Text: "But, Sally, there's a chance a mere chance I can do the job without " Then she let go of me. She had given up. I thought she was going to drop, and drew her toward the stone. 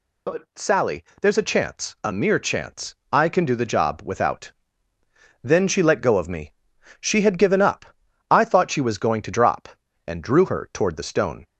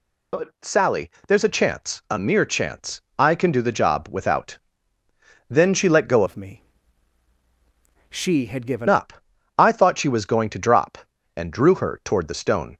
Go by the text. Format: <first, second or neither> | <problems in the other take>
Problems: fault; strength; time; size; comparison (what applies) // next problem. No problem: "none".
first | pauses between "chance" and "I"; slight; at 2.9 s; 0.20 s long; slight in the first // changes voice from "of" to "given"; from 6.2 to 8.8 s; 2.6 s long